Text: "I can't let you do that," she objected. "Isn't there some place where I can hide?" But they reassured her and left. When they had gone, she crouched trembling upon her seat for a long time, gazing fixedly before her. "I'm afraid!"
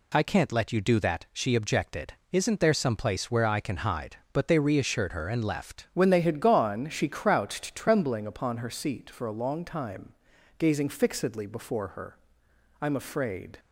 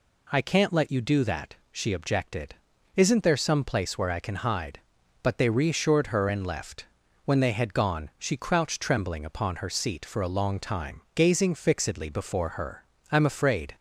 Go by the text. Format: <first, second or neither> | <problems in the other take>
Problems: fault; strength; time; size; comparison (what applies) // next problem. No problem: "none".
second | changes voice at "When"; from 5.9 s on; 7.6 s long